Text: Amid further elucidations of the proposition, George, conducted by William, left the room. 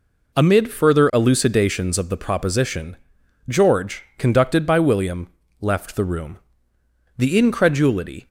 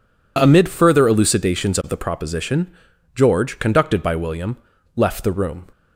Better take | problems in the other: second | goes on to say "The incredulity"; noticeable; from 7.1 s on; 1.1 s long

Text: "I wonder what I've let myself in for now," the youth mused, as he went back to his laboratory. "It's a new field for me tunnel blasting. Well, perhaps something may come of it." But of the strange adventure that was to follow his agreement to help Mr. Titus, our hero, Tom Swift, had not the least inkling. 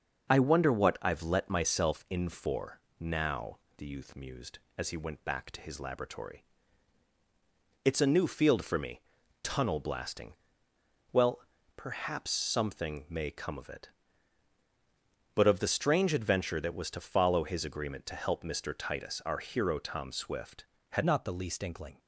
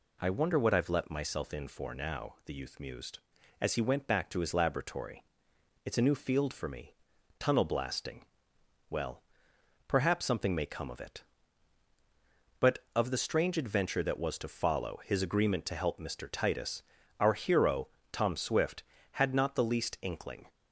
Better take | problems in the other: second | starts louder than the rest; until 1.3 s; 6 dB // pauses between "for" and "now"; slight; at 2.8 s; 0.18 s long // pauses between "me" and "tunnel"; at 8.9 s; 0.42 s long; also in the second // changes voice at "not"; from 21.0 s on; 0.9 s long

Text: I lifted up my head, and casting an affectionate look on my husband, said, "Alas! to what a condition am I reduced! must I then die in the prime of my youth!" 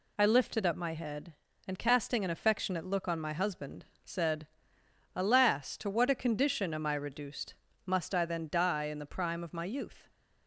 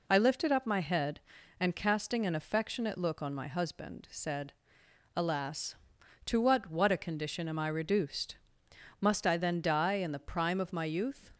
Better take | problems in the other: first | says "what" twice; at 6.6 s

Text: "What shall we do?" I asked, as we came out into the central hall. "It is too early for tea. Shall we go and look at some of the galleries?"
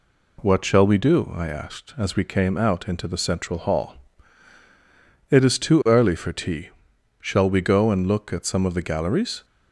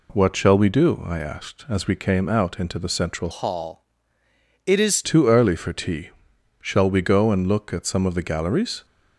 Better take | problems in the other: first | changes voice from "hall" to "is"; from 3.3 to 5.0 s; 1.7 s long

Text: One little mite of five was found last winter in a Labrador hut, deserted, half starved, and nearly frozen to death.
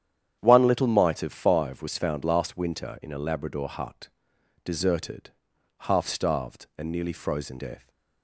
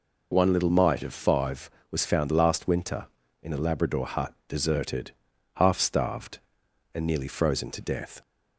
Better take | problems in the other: second | starts louder than the rest; strong; until 1.4 s; 9.5 dB // skips "to"; at 7.5 s

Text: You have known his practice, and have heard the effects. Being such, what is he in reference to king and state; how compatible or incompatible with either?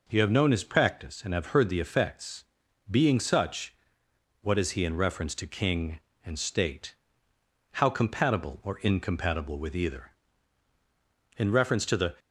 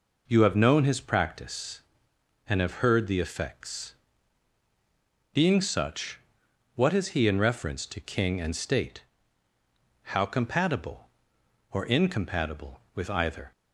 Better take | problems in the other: second | goes on to say "In reference to the"; noticeable; from 11.3 s on; 0.78 s long

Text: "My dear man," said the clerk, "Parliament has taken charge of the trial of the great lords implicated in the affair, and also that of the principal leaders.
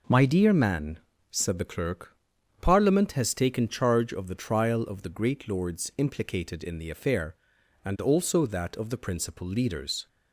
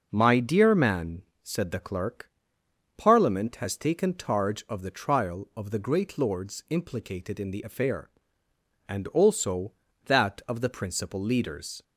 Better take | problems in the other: neither | none

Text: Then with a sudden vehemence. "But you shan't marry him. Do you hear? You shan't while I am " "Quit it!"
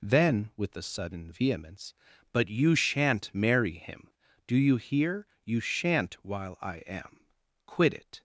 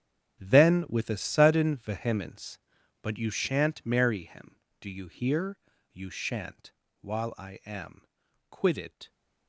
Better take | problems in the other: first | gets quieter; strong; throughout; 18.5 dB // pauses between "shan't" and "while"; slight; at 6.7 s; 0.30 s long

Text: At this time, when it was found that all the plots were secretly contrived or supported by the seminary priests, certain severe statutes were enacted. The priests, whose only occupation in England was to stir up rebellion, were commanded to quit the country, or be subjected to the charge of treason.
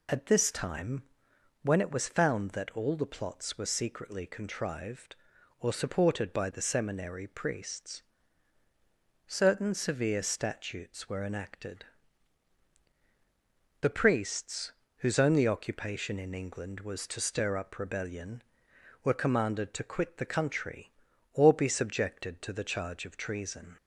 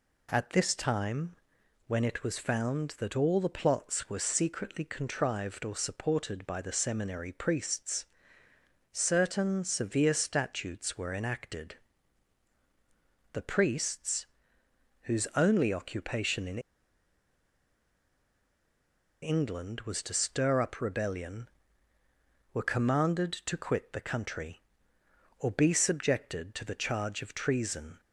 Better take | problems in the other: first | pauses between "in" and "England"; strong; at 16.5 s; 2.6 s long

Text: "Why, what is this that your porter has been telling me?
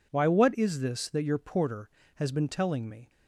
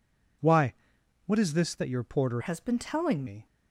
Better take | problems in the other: first | changes voice from "has" to "telling"; from 2.4 to 3.2 s; 0.8 s long

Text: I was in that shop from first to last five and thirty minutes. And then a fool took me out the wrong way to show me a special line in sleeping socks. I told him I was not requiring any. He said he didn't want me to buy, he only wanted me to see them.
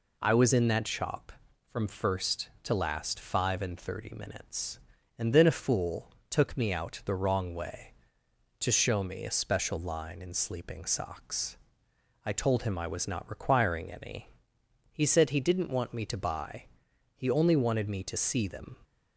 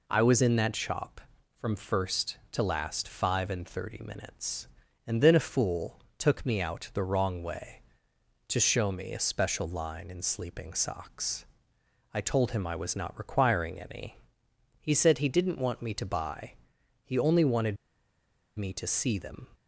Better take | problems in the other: first | pauses between "fool" and "took"; slight; at 5.9 s; 0.18 s long; slight in the first // pauses between "wanted" and "me"; noticeable; at 17.7 s; 0.81 s long

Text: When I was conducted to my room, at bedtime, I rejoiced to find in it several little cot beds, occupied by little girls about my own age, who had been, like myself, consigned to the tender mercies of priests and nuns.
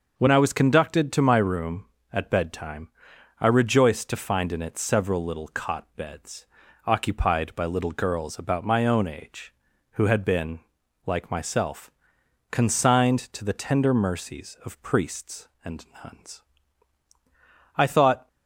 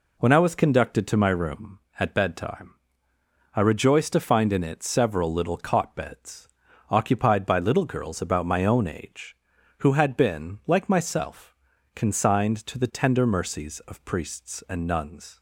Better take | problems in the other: second | starts louder than the rest; noticeable; until 1.2 s; 6 dB // pauses between "and" and "nuns"; slight; at 15.8 s; 0.18 s long // goes on to say "I thought"; from 17.7 s on; 0.50 s long

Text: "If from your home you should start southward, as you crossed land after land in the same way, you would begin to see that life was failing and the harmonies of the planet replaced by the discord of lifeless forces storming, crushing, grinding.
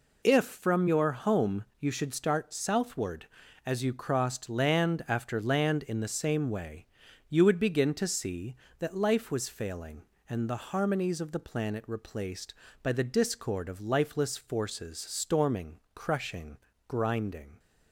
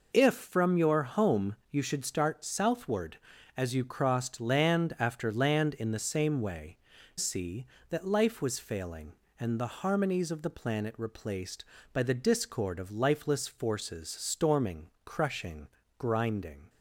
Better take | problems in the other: first | skips "you would begin to"; at 6.9 s

